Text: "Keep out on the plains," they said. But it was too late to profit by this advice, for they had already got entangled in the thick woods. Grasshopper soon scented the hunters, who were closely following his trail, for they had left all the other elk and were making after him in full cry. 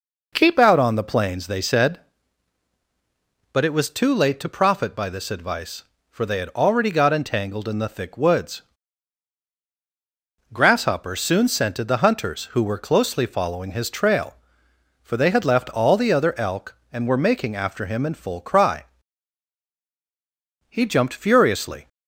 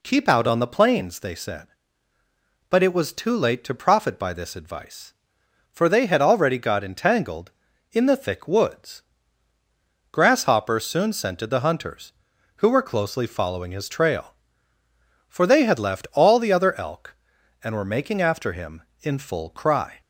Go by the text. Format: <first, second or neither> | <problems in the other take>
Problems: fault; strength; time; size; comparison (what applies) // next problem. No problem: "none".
second | goes on to say "He jumped furiously"; noticeable; from 20.6 s on; 1.2 s long